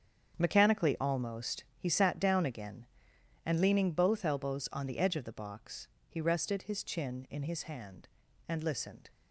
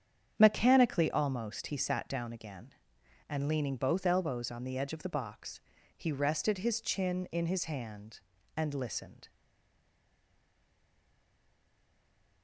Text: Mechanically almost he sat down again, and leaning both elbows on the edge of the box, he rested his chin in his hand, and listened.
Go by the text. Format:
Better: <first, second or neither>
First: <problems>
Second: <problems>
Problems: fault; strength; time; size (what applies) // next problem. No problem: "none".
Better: first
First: starts louder than the rest; strong; until 1.4 s; 8 dB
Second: starts louder than the rest; strong; until 1.3 s; 8.5 dB // stays silent after the last word; strong; from 9.2 s on; 3.2 s long